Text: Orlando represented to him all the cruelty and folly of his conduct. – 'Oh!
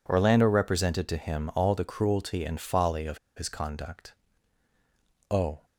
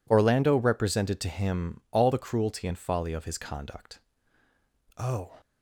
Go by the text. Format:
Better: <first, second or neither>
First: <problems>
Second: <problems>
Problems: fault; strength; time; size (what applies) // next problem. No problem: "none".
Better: second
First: pauses between "of" and "his"; slight; at 3.1 s; 0.18 s long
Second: none